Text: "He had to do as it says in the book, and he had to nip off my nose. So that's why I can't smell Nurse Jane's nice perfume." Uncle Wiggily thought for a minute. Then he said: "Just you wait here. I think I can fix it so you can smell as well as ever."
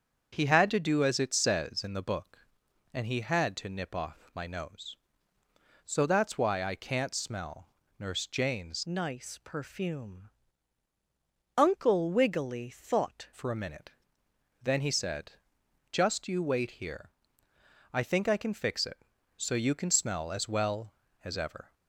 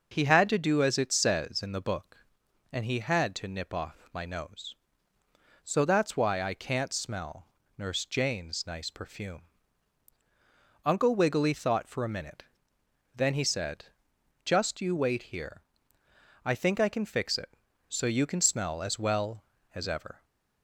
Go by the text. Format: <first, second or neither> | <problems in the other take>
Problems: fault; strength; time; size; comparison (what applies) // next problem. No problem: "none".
second | starts louder than the rest; strong; until 1.3 s; 7 dB // pauses between "smell" and "Nurse"; slight; at 7.6 s; 0.32 s long; slight in the second // changes voice from "nice" to "thought"; from 8.8 to 13.2 s; 4.4 s long